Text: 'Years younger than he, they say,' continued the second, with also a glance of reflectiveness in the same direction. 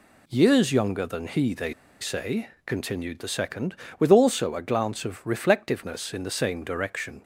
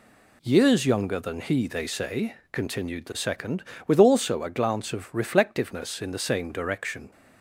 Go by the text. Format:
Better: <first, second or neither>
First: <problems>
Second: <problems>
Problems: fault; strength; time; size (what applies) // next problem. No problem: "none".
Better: second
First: pauses between "they" and "say"; slight; at 1.7 s; 0.29 s long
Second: none